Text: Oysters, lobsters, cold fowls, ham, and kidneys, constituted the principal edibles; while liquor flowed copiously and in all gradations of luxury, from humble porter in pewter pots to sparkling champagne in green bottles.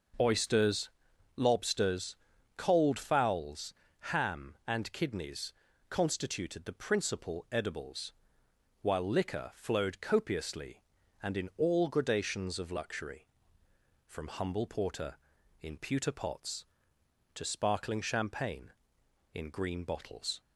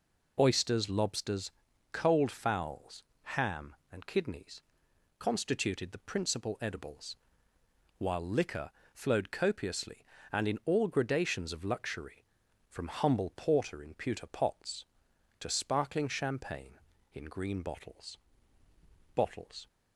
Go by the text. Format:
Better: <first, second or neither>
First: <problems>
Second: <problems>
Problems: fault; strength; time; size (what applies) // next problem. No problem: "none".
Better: first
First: none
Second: pauses between "liquor" and "flowed"; slight; at 8.7 s; 0.24 s long // says "bottles" twice; at 19.1 s